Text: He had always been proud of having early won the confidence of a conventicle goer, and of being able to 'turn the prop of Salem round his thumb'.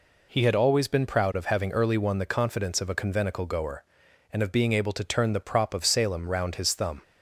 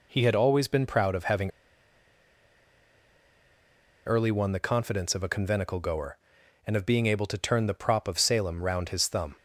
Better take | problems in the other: first | pauses between "having" and "early"; strong; at 1.5 s; 2.5 s long

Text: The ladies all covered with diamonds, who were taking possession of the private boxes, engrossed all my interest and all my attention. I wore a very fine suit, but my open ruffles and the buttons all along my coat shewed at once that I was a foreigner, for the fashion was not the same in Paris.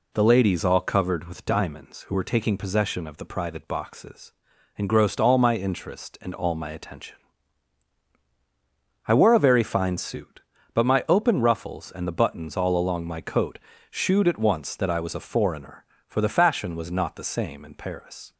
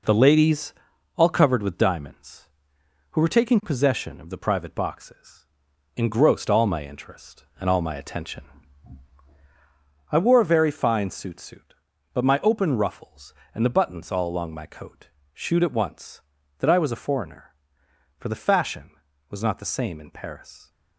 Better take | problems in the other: first | pauses between "ladies" and "all"; at 0.7 s; 0.42 s long // says "suit" twice; at 11.4 s // pauses between "coat" and "shewed"; slight; at 15.0 s; 0.26 s long; slight in the first

